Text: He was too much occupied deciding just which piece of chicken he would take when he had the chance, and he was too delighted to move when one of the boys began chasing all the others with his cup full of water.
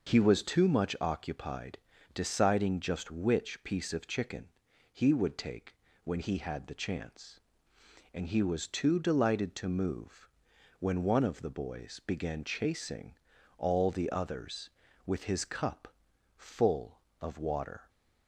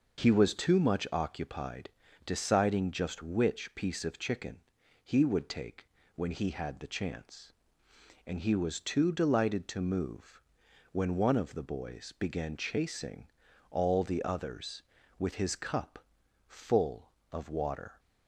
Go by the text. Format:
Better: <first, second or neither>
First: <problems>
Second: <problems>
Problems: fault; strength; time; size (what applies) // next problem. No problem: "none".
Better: neither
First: pauses between "occupied" and "deciding"; slight; at 1.7 s; 0.34 s long // pauses between "chicken" and "he"; noticeable; at 4.4 s; 0.46 s long // pauses between "take" and "when"; slight; at 5.7 s; 0.30 s long // pauses between "move" and "when"; noticeable; at 10.2 s; 0.50 s long // pauses between "chasing" and "all"; at 13.1 s; 0.42 s long // pauses between "cup" and "full"; noticeable; at 15.8 s; 0.48 s long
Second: pauses between "occupied" and "deciding"; slight; at 1.9 s; 0.34 s long // pauses between "chicken" and "he"; noticeable; at 4.5 s; 0.46 s long // pauses between "take" and "when"; slight; at 5.8 s; 0.30 s long // pauses between "move" and "when"; noticeable; at 10.4 s; 0.50 s long // pauses between "chasing" and "all"; at 13.2 s; 0.42 s long // pauses between "cup" and "full"; noticeable; at 15.9 s; 0.48 s long